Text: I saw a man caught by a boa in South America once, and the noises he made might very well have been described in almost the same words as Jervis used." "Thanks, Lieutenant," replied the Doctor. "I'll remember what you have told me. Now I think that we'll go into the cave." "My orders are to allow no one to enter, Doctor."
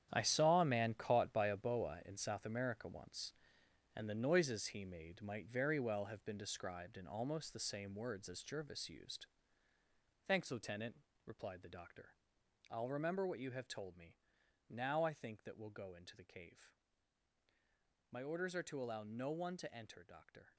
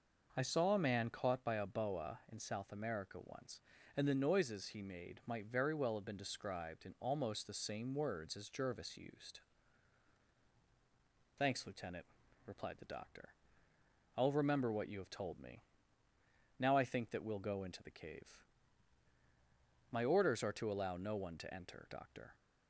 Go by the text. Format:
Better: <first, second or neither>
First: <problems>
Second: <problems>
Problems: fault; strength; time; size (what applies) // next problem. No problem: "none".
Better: second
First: gets quieter; strong; throughout; 12.5 dB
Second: none